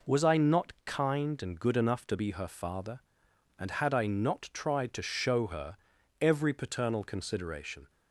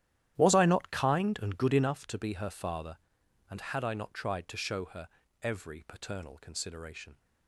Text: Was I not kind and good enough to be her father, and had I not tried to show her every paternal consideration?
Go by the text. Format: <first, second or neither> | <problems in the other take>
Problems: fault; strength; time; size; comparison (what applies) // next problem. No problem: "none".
first | starts louder than the rest; strong; until 2.0 s; 12 dB // pauses between "her" and "every"; slight; at 5.0 s; 0.36 s long; noticeable in the first